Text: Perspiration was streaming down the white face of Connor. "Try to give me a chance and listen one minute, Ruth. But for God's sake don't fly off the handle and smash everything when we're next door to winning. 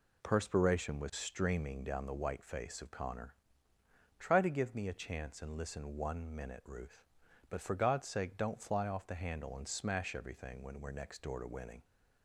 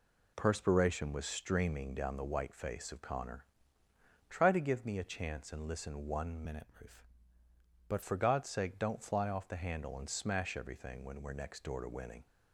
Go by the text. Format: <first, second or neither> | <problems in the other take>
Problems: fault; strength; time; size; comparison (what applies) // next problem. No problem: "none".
first | changes voice from "minute" to "But"; from 6.4 to 8.0 s; 1.6 s long